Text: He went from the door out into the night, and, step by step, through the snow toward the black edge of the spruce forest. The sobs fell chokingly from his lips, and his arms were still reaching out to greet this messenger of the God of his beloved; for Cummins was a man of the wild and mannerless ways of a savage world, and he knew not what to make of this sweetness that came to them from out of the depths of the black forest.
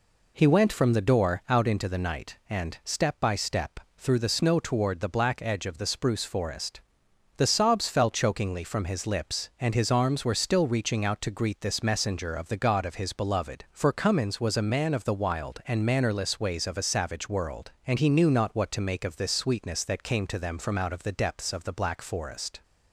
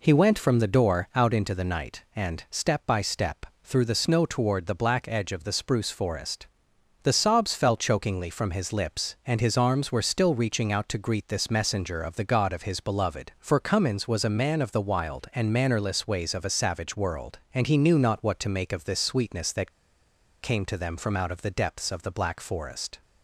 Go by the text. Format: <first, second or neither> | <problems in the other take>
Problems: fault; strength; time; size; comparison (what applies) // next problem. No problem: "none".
first | pauses between "that" and "came"; noticeable; at 19.7 s; 0.71 s long